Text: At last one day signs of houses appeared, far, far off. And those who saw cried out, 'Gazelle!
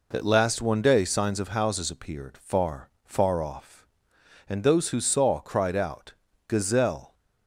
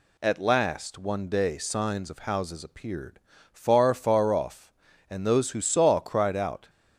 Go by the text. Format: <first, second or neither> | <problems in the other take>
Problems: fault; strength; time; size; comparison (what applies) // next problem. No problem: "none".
first | stops before "Gazelle"; at 6.6 s